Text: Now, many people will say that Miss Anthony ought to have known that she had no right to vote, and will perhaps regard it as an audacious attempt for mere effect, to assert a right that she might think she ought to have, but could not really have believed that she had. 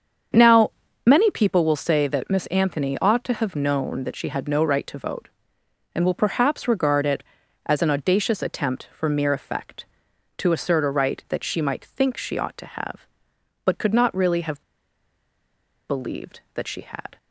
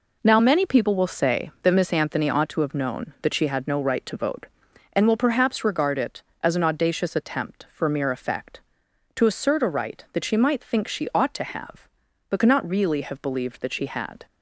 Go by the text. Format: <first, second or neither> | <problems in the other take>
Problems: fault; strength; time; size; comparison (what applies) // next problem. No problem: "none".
second | starts louder than the rest; strong; until 1.7 s; 7 dB // pauses between "have" and "believed"; strong; at 14.6 s; 1.2 s long